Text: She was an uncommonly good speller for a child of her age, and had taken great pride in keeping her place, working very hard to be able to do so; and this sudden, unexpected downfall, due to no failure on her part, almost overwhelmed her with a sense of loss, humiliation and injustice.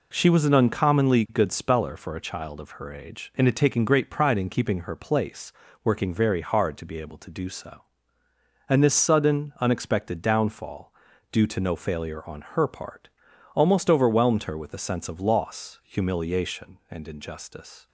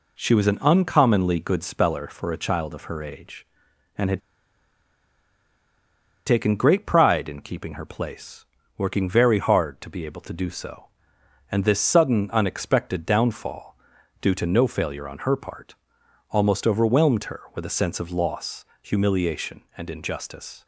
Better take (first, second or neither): first